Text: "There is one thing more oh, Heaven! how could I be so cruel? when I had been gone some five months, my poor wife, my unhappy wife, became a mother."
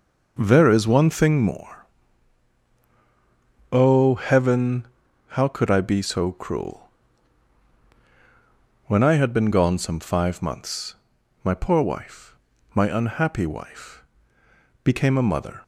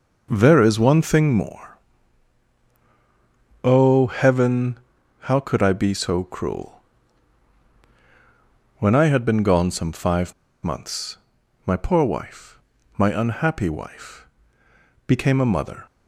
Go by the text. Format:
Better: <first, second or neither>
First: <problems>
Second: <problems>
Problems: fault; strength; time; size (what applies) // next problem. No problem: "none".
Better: first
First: pauses between "more" and "oh"; strong; at 1.8 s; 1.8 s long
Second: pauses between "more" and "oh"; strong; at 1.7 s; 1.8 s long // pauses between "five" and "months"; slight; at 10.3 s; 0.31 s long